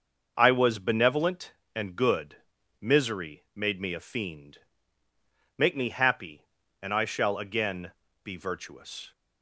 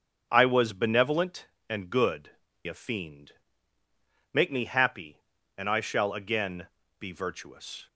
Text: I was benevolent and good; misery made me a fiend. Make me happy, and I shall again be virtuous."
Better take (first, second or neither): first